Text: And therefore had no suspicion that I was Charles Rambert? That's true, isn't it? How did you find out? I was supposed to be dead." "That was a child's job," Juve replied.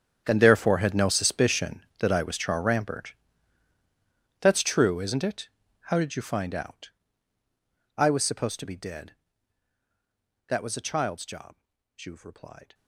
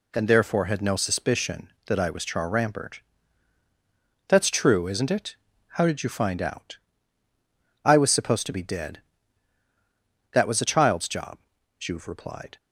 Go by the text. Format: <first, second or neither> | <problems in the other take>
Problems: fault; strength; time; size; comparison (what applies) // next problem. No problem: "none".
second | gets quieter; strong; throughout; 17.5 dB